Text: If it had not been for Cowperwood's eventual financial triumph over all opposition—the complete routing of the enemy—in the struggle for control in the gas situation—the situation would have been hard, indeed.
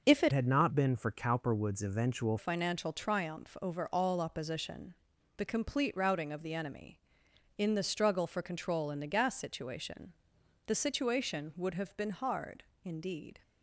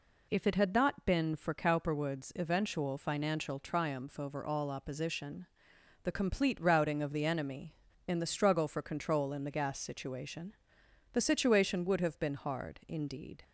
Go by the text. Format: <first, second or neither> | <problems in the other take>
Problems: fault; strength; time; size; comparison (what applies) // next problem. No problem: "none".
second | changes voice from "had" to "eventual"; from 0.3 to 2.3 s; 2.0 s long